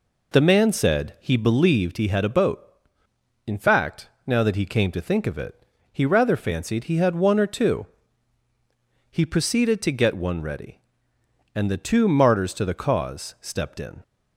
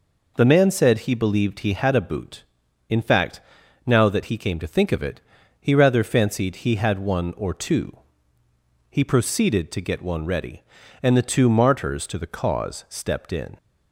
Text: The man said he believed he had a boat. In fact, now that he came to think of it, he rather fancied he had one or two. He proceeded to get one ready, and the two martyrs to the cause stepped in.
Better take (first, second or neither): first